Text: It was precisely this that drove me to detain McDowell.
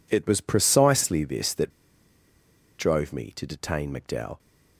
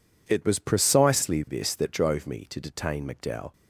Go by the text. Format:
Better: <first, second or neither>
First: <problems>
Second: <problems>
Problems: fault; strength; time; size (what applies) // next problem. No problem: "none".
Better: second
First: pauses between "that" and "drove"; at 1.6 s; 1.0 s long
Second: none